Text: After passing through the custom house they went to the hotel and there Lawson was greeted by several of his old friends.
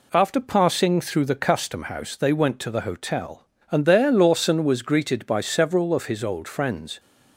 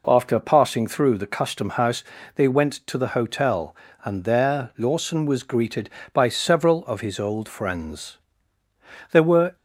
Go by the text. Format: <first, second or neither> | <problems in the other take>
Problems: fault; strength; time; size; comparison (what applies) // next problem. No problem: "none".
first | pauses between "house" and "they"; slight; at 2.0 s; 0.32 s long // goes on to say "There were"; slight; from 9.1 s on; 0.44 s long